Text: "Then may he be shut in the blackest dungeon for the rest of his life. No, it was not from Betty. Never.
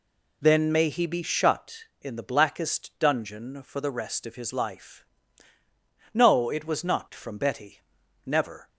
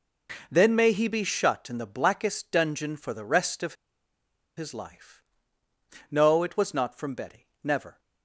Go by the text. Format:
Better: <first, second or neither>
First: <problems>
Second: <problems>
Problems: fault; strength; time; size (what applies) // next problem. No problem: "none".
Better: first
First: none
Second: pauses between "of" and "his"; noticeable; at 3.7 s; 0.84 s long